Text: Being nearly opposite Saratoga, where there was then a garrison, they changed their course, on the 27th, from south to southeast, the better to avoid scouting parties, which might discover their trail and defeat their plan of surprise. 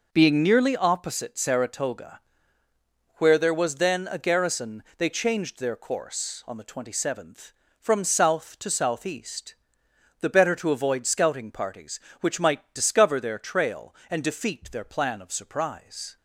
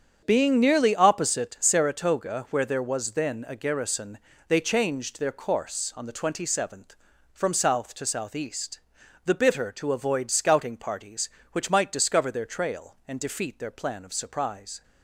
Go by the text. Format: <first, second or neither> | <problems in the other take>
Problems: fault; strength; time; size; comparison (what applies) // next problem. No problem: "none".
first | starts louder than the rest; strong; until 1.2 s; 7.5 dB // says "bitter" for "better"; at 9.3 s